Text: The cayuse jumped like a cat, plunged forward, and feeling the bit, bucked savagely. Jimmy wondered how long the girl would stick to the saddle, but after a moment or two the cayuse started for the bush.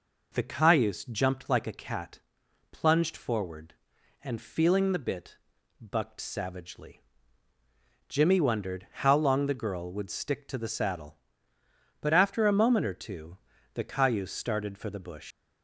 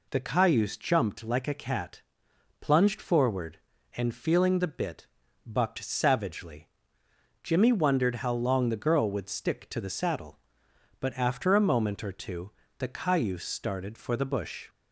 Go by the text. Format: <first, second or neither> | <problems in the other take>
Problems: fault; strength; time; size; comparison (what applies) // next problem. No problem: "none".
second | pauses between "two" and "the"; at 13.3 s; 0.38 s long; slight in the second // leaves "bush" unfinished; at 15.3 s; 120 ms